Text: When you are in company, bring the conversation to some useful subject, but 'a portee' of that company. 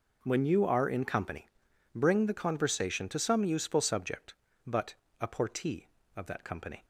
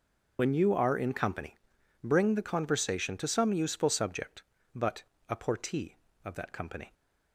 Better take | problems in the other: first | loses the start of "When"; at 0.3 s; 80 ms // pauses between "but" and "a"; slight; at 5.0 s; 0.26 s long; slight in the first

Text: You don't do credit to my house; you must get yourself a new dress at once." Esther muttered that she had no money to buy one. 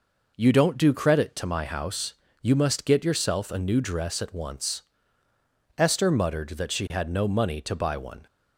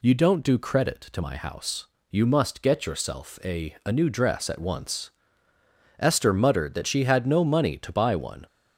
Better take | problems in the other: first | says "a" twice; at 3.8 s

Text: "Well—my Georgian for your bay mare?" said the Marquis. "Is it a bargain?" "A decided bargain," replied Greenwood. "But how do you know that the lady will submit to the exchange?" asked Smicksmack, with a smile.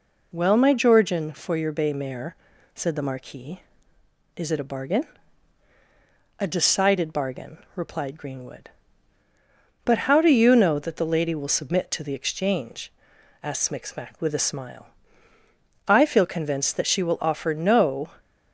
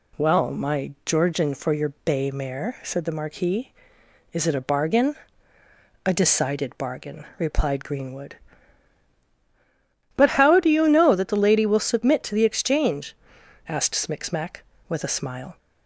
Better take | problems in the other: second | goes on to say "I feel convinced that she will offer no"; strong; from 15.8 s on; 2.2 s long

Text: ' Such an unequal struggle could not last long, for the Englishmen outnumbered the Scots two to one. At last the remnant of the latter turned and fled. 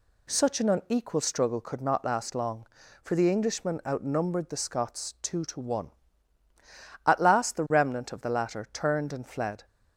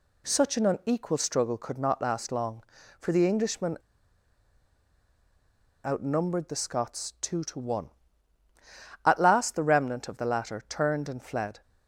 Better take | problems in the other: first | pauses between "Englishmen" and "outnumbered"; strong; at 3.7 s; 2.0 s long

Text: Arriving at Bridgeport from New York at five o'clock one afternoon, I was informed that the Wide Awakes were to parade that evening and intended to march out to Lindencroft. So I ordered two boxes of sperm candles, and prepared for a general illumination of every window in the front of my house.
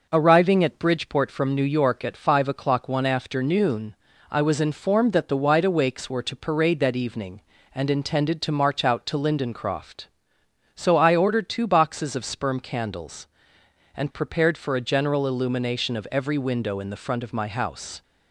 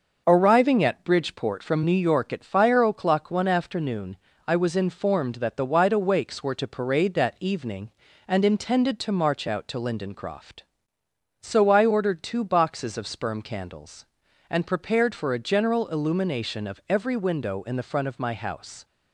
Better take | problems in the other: first | starts louder than the rest; noticeable; until 1.2 s; 6 dB // says "fire" for "five"; at 2.4 s

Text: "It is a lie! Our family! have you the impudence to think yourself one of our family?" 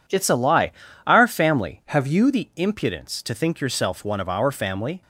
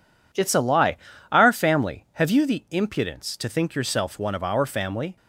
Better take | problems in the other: second | changes voice from "have" to "you"; from 1.9 to 2.3 s; 0.4 s long

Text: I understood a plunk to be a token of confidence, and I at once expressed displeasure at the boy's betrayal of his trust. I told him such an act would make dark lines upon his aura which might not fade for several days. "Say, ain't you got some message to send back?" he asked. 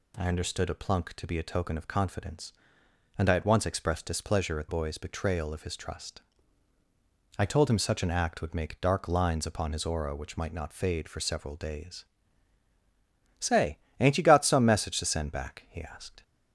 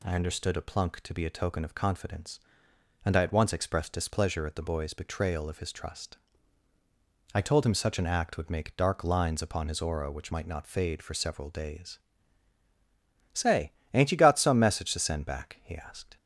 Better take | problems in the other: second | skips "the"; at 4.6 s

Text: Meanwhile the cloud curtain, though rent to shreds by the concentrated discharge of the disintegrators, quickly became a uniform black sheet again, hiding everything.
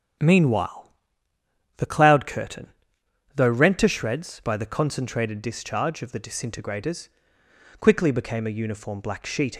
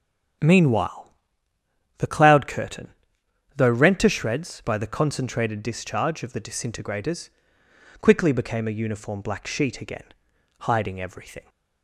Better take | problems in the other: second | starts louder than the rest; until 2.0 s; 6.5 dB; also in the second // pauses between "Meanwhile" and "the"; noticeable; at 0.8 s; 0.86 s long; noticeable in the second // stops before "again hiding everything"; at 9.5 s

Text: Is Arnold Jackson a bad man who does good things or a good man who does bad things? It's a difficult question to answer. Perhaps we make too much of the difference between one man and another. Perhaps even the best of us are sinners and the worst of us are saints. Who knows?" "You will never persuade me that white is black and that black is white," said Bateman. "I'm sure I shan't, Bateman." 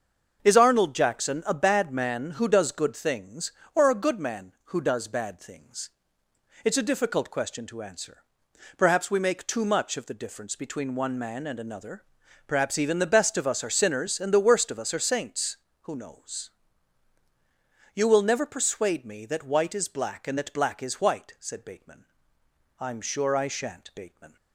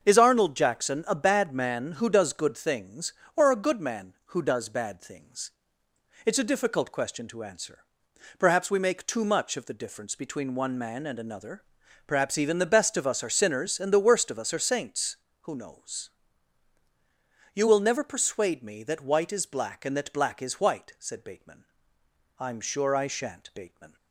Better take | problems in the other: neither | starts louder than the rest; the same in both

